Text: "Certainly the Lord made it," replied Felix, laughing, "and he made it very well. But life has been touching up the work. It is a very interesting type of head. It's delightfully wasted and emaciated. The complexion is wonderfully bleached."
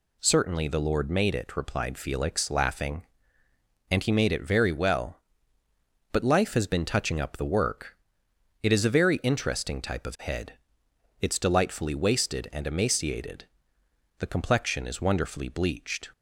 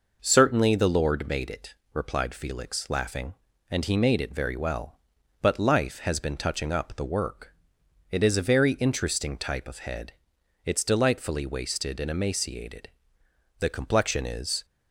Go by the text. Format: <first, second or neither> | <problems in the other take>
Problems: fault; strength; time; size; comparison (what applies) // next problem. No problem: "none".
first | stops before "wonderfully bleached"; at 14.6 s